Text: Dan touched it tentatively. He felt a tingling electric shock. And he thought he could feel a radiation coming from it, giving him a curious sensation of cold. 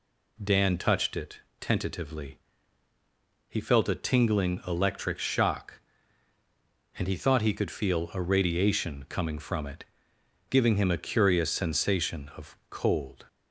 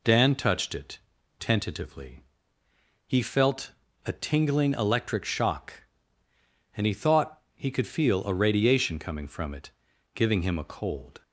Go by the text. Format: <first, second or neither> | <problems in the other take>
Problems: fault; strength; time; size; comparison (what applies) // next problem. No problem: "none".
first | pauses between "it" and "tentatively"; at 0.9 s; 0.40 s long; slight in the first // pauses between "felt" and "a"; slight; at 3.7 s; 0.32 s long // skips "curious sensation of"; at 10.6 s